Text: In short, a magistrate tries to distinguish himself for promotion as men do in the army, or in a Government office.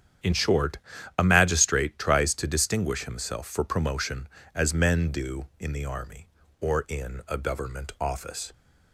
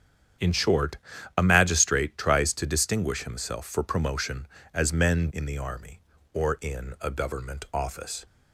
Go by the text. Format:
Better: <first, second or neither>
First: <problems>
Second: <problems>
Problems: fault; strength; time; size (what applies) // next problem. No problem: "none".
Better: first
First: starts louder than the rest; strong; until 1.6 s; 9.5 dB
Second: starts louder than the rest; strong; until 1.8 s; 8.5 dB // skips "do"; at 5.3 s